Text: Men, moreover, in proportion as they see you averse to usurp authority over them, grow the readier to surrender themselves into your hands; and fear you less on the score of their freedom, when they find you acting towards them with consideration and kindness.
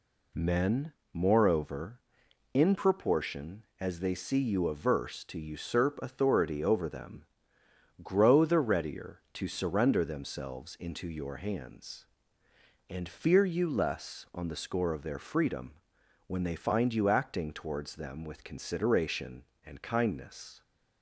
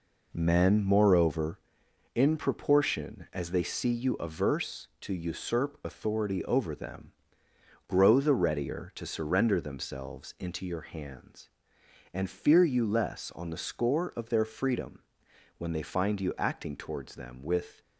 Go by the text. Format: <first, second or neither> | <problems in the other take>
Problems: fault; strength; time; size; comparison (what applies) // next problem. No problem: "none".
first | stops before "consideration and kindness"; at 17.8 s